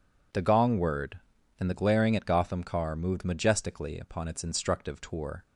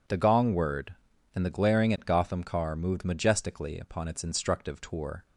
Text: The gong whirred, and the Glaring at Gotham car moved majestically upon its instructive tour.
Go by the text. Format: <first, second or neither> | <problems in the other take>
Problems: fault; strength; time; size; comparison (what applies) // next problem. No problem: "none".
neither | none